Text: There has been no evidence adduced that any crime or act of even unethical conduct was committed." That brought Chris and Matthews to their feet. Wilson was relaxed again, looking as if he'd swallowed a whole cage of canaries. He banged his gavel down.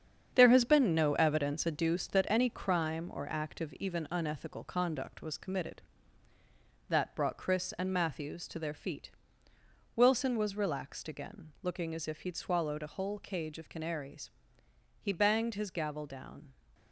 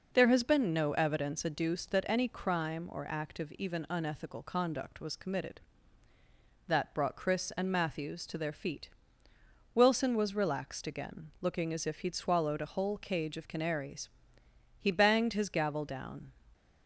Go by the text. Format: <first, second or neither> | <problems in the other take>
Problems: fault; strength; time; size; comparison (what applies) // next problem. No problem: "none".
second | gets quieter; strong; throughout; 8 dB